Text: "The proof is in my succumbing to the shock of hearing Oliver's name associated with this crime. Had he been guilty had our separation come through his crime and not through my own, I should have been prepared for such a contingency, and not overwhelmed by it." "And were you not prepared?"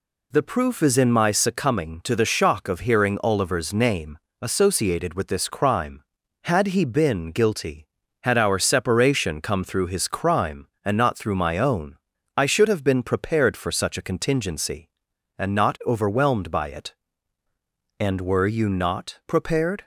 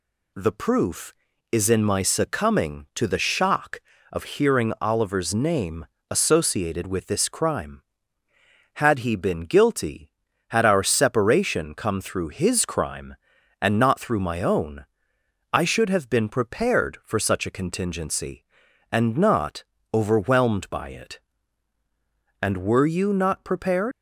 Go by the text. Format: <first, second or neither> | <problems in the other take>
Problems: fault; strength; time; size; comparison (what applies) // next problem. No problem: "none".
first | pauses between "name" and "associated"; slight; at 5.8 s; 0.24 s long; slight in the first // pauses between "not" and "overwhelmed"; slight; at 19.6 s; 0.30 s long // leaves "prepared" unfinished; at 23.9 s; 85 ms